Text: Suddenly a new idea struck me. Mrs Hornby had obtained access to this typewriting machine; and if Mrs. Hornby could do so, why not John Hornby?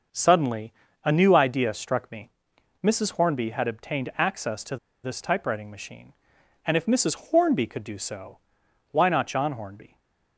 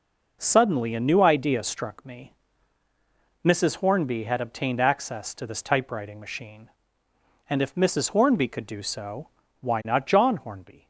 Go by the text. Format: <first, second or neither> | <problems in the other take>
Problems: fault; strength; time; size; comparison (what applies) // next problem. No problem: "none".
second | starts louder than the rest; until 1.4 s; 6 dB // pauses between "Suddenly" and "a"; slight; at 0.7 s; 0.32 s long // pauses between "to" and "this"; slight; at 4.7 s; 0.27 s long // stays silent after the last word; slight; from 9.8 s on; 0.5 s long